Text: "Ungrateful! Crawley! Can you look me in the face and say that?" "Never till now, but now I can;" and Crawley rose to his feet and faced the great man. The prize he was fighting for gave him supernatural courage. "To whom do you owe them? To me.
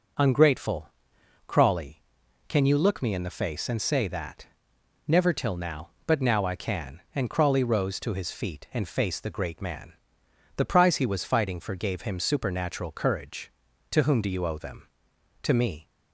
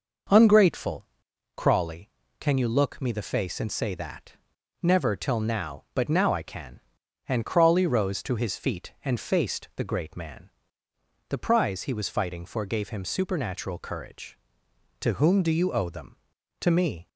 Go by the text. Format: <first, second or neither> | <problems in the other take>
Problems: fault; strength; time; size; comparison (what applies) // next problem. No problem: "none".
first | skips "in"; at 3.1 s